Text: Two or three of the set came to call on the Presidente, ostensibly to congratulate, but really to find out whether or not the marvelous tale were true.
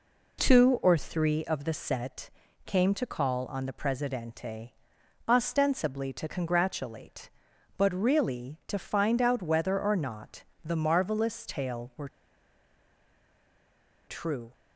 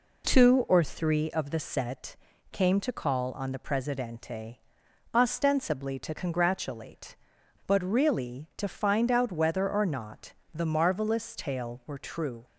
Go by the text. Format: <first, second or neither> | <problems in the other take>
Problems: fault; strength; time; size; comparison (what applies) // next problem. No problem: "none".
second | pauses between "set" and "came"; slight; at 2.2 s; 0.36 s long; slight in the second // pauses between "not" and "the"; slight; at 10.4 s; 0.20 s long; slight in the second // pauses between "were" and "true"; strong; at 12.0 s; 1.9 s long